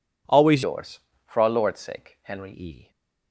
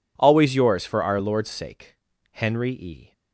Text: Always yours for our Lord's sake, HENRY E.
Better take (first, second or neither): second